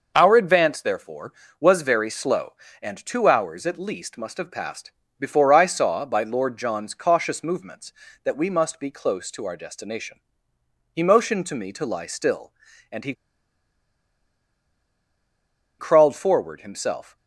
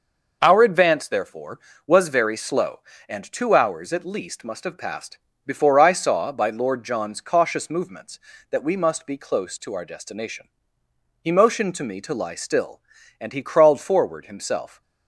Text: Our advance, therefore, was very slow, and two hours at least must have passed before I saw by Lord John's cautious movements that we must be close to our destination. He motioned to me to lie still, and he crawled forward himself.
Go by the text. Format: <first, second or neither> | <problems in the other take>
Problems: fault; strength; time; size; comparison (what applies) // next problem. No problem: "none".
second | pauses between "passed" and "before"; slight; at 4.9 s; 0.30 s long; slight in the second // pauses between "he" and "crawled"; strong; at 13.1 s; 2.6 s long